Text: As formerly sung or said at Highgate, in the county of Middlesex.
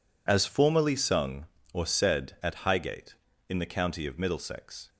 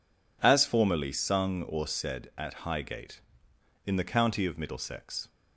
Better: second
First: loses the start of "As"; at 0.2 s; 25 ms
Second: none

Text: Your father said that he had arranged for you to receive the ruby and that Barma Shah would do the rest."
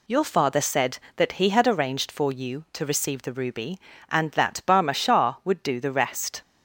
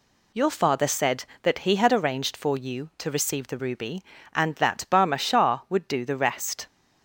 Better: neither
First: none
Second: none

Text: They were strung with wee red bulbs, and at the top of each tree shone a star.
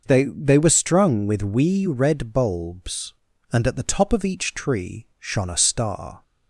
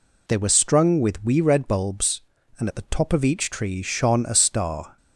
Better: second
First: says "They" twice; at 0.2 s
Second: none

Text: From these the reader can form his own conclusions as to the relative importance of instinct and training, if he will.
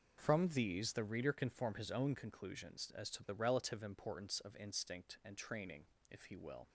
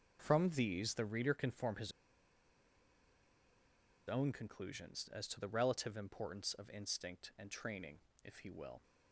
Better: first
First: none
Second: pauses between "his" and "own"; strong; at 1.9 s; 2.1 s long

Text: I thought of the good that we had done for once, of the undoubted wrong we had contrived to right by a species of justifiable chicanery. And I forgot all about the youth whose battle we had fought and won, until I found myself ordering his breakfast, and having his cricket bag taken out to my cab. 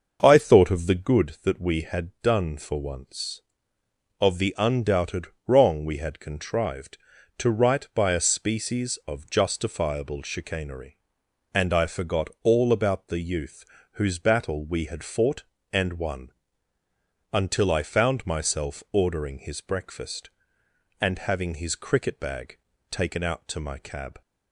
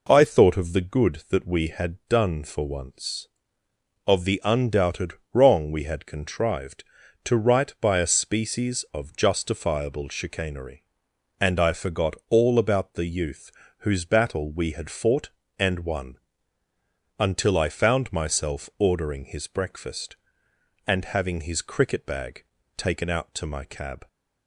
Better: second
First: starts louder than the rest; until 1.3 s; 6.5 dB // pauses between "undoubted" and "wrong"; slight; at 5.2 s; 0.22 s long // pauses between "youth" and "whose"; slight; at 13.6 s; 0.28 s long // pauses between "bag" and "taken"; slight; at 22.5 s; 0.32 s long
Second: pauses between "undoubted" and "wrong"; slight; at 5.1 s; 0.22 s long // pauses between "youth" and "whose"; slight; at 13.5 s; 0.28 s long // pauses between "bag" and "taken"; slight; at 22.4 s; 0.32 s long

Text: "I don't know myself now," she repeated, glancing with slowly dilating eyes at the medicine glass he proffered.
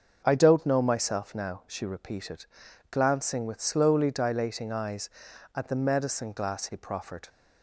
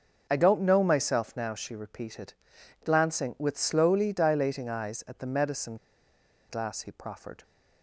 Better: first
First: starts louder than the rest; until 1.2 s; 6.5 dB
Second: starts louder than the rest; until 1.3 s; 6.5 dB // pauses between "medicine" and "glass"; noticeable; at 5.7 s; 0.73 s long

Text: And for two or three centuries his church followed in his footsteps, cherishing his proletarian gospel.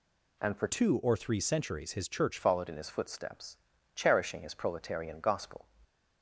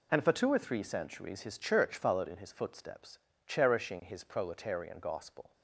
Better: second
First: changes voice from "two" to "church"; from 0.6 to 2.3 s; 1.7 s long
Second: none

